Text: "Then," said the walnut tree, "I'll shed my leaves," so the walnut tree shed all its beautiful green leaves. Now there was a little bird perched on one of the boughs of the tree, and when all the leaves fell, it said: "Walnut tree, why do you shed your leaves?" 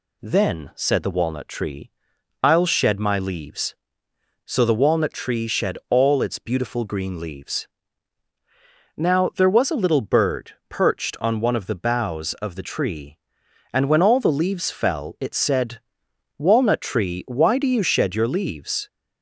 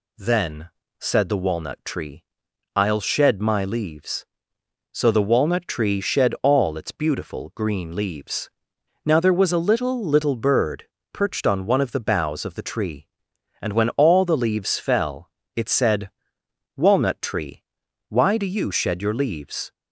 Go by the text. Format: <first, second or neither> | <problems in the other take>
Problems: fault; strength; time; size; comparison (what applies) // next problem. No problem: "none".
first | says "little" twice; at 10.0 s // pauses between "bird" and "perched"; slight; at 10.8 s; 0.26 s long